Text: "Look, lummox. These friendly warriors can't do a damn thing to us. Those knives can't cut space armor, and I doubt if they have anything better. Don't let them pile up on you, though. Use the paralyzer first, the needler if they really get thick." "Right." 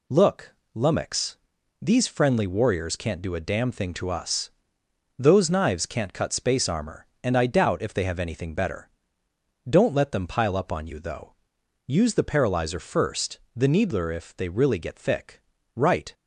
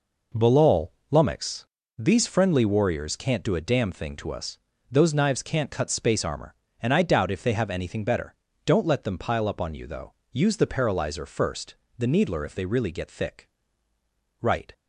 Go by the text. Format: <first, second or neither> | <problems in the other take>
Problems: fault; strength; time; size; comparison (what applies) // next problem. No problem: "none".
first | says "Balal" for "Look"; at 0.3 s